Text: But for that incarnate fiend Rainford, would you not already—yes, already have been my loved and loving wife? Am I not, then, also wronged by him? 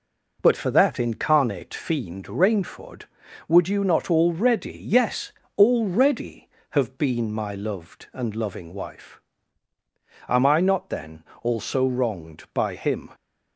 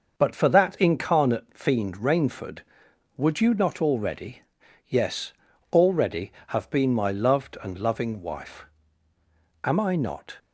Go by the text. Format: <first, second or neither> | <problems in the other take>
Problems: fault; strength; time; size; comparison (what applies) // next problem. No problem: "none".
first | stops before "then also wronged by him"; at 10.3 s